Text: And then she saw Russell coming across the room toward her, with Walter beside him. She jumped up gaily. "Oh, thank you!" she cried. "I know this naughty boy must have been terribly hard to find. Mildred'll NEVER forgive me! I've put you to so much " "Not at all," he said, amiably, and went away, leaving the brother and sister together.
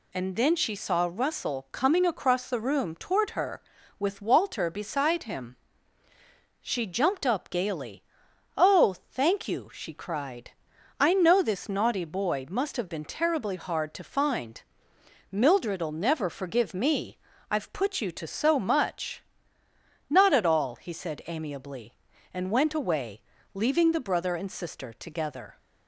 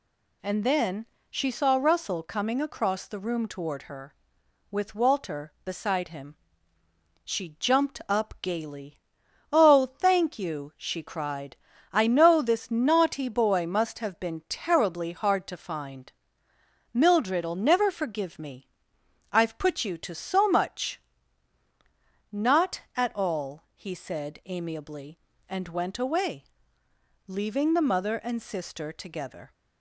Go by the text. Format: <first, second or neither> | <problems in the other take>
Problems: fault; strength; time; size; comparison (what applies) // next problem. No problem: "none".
first | pauses between "then" and "she"; slight; at 1.0 s; 0.24 s long // says "mother" for "brother"; at 27.8 s